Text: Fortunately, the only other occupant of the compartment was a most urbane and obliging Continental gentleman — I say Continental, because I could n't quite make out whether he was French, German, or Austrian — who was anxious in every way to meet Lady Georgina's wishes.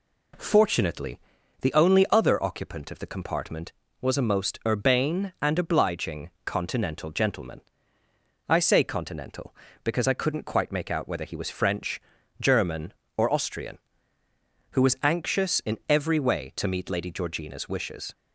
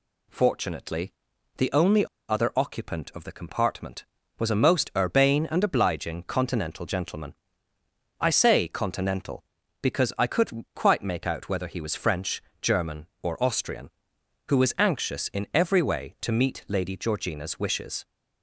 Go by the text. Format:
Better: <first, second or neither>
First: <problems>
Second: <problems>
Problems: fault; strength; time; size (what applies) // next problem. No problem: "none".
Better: first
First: none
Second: pauses between "only" and "other"; slight; at 2.0 s; 0.23 s long